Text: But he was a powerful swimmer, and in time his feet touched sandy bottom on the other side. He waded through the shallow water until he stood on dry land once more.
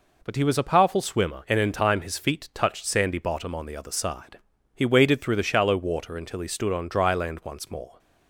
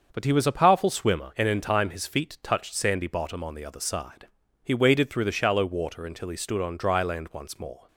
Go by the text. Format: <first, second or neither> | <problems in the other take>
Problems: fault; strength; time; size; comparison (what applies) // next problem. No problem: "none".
first | starts louder than the rest; until 1.4 s; 6.5 dB